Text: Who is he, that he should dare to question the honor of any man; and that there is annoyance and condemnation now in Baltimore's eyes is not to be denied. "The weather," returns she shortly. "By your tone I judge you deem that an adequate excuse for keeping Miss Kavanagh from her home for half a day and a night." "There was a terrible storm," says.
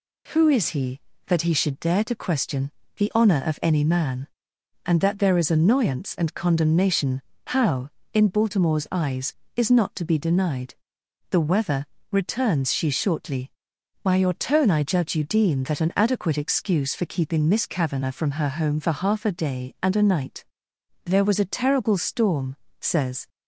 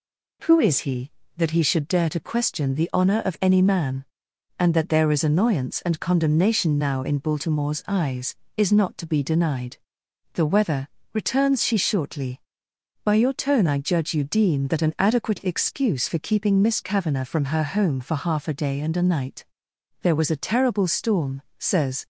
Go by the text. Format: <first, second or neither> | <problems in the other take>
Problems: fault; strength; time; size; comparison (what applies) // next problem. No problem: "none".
second | pauses between "question" and "the"; slight; at 2.7 s; 0.24 s long // says "how" for "now"; at 7.4 s